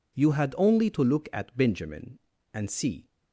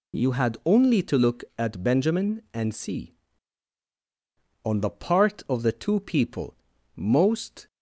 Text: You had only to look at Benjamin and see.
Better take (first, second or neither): first